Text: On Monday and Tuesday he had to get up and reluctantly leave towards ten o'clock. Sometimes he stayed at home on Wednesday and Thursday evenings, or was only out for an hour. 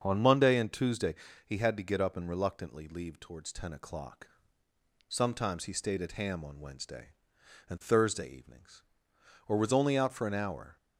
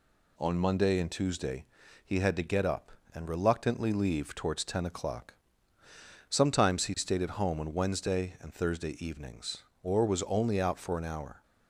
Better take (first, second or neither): second